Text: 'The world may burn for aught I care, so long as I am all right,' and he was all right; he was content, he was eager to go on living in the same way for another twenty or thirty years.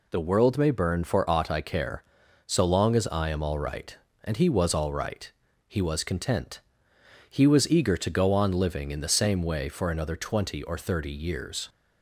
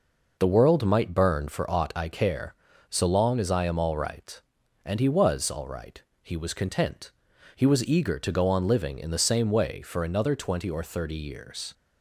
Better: first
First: none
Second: says "might" for "may"; at 0.8 s

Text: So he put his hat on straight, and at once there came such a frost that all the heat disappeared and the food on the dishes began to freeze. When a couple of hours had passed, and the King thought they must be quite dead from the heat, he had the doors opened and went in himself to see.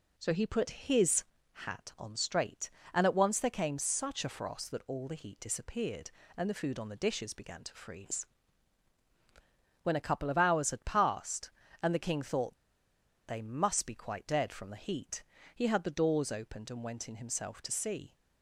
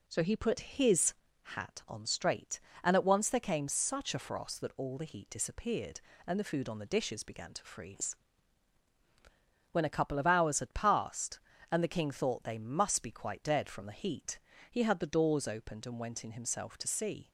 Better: second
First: pauses between "his" and "hat"; slight; at 1.2 s; 0.30 s long // pauses between "thought" and "they"; noticeable; at 12.5 s; 0.72 s long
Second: pauses between "his" and "hat"; slight; at 1.1 s; 0.30 s long

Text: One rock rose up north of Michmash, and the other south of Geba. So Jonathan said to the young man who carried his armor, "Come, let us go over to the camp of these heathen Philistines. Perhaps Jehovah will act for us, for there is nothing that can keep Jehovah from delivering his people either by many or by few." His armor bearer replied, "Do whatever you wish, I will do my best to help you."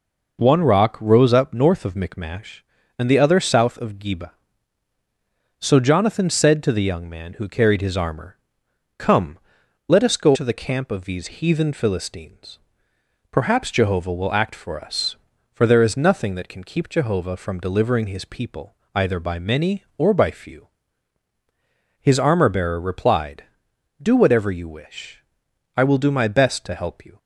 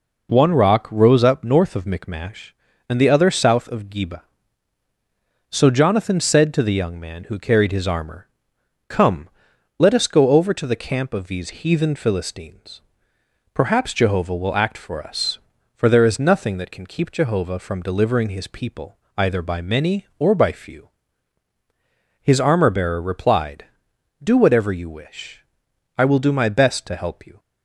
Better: second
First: skips "over"; at 10.3 s // pauses between "people" and "either"; slight; at 18.7 s; 0.22 s long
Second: pauses between "people" and "either"; slight; at 18.9 s; 0.22 s long

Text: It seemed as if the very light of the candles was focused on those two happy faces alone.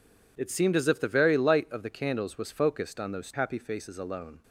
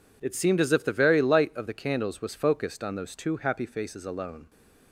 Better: second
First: skips "two"; at 3.3 s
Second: none

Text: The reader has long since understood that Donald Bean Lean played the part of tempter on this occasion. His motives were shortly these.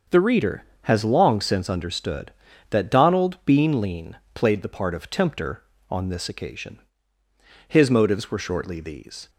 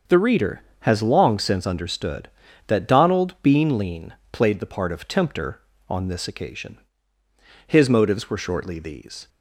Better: neither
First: starts louder than the rest; until 1.3 s; 6.5 dB // pauses between "Lean" and "played"; slight; at 4.1 s; 0.19 s long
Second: starts louder than the rest; until 1.2 s; 6.5 dB // pauses between "Lean" and "played"; slight; at 4.1 s; 0.20 s long

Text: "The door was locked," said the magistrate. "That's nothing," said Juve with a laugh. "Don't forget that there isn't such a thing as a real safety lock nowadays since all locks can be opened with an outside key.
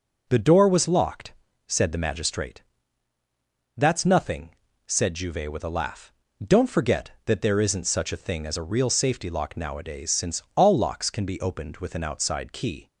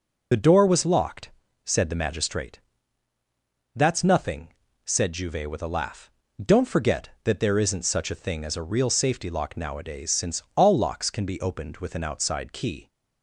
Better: first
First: none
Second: loses the start of "The"; at 0.3 s; 45 ms

